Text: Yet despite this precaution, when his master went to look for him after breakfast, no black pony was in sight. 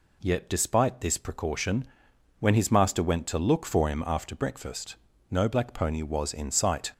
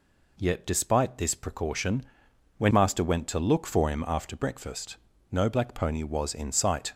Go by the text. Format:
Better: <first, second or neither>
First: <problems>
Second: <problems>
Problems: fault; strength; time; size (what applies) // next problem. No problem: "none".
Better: first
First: none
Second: skips "his"; at 2.7 s